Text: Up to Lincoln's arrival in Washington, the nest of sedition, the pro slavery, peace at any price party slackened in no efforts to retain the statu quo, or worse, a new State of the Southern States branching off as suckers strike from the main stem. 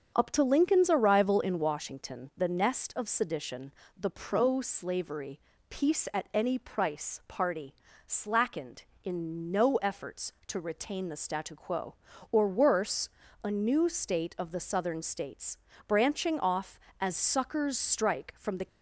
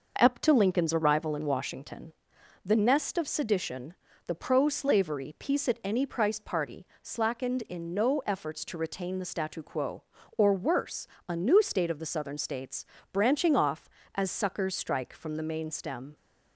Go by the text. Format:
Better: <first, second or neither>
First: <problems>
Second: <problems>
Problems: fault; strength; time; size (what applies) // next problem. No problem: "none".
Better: second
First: starts louder than the rest; strong; until 1.1 s; 7.5 dB // pauses between "party" and "slackened"; slight; at 7.7 s; 0.32 s long // pauses between "States" and "branching"; slight; at 15.5 s; 0.30 s long // stops before "main stem"; at 18.6 s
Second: pauses between "party" and "slackened"; slight; at 6.8 s; 0.16 s long // pauses between "States" and "branching"; slight; at 12.8 s; 0.26 s long